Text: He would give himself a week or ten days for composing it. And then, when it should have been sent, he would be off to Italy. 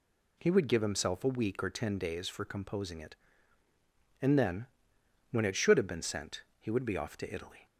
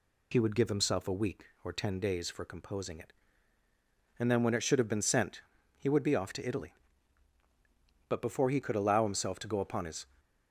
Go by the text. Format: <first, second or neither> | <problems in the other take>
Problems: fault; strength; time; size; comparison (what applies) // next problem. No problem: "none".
first | goes on to say "But before he could allow himself to go upon his"; strong; from 8.0 s on; 1.9 s long